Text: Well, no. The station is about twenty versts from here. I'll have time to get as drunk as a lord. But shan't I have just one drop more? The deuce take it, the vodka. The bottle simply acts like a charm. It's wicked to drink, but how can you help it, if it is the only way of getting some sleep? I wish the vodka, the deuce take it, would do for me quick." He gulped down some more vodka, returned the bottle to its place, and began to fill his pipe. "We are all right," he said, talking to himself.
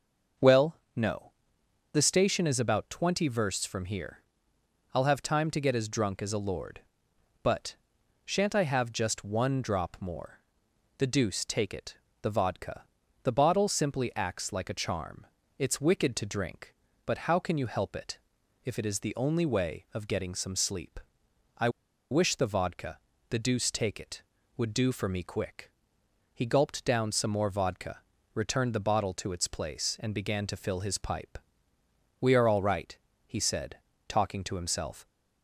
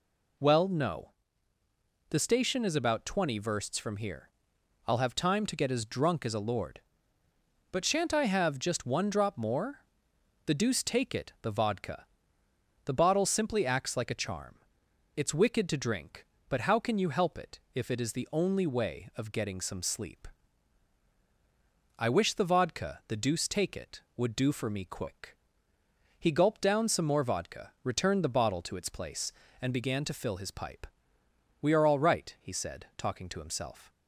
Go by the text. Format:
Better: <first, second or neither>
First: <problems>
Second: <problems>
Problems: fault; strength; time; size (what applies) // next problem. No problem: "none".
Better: second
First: starts louder than the rest; noticeable; until 2.2 s; 6 dB // pauses between "But" and "shan't"; noticeable; at 7.7 s; 0.48 s long // pauses between "I" and "wish"; at 21.6 s; 0.41 s long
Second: none